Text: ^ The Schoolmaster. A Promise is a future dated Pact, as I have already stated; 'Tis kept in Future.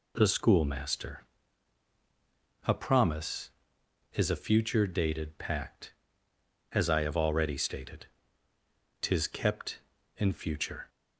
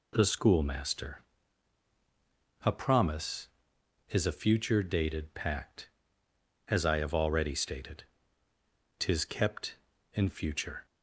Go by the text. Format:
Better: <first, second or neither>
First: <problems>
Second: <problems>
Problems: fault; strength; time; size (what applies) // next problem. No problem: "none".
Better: neither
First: none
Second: none